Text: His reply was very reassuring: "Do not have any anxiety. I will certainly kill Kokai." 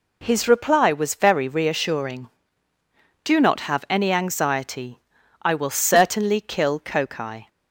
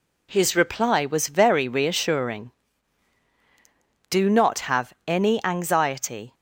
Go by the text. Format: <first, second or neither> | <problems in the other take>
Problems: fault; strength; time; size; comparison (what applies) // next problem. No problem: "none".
first | stops before "I will certainly kill Kokai"; at 6.3 s